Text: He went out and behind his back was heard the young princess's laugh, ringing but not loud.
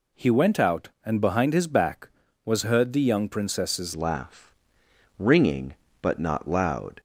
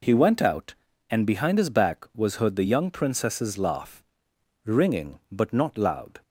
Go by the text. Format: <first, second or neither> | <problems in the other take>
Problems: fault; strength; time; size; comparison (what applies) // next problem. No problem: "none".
second | changes voice at "laugh"; from 3.9 s on; 3.0 s long